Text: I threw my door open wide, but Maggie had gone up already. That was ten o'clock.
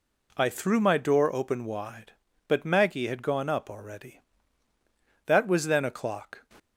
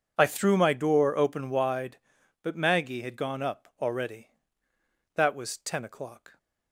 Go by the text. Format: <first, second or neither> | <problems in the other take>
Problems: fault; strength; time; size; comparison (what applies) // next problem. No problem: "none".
second | says "then" for "ten"; at 5.6 s